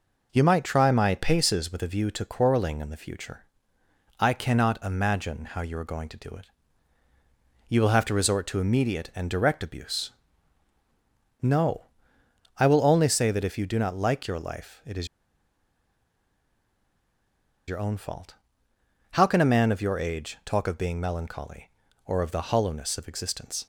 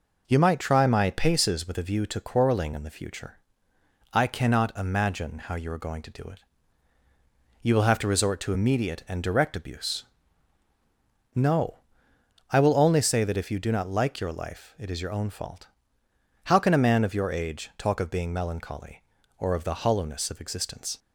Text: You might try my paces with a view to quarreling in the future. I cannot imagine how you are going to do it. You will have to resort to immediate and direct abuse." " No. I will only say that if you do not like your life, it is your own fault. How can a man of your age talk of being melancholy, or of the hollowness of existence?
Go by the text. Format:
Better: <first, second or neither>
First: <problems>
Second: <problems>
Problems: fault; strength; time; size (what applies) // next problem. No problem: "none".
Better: second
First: pauses between "is" and "your"; strong; at 15.0 s; 2.6 s long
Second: none